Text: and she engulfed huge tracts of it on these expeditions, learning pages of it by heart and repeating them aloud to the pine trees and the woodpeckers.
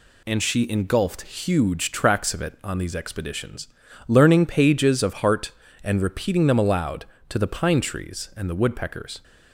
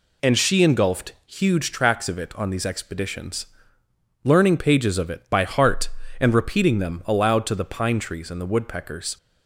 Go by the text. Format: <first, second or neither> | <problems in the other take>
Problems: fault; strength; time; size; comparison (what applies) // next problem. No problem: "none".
second | skips "it by"; at 5.1 s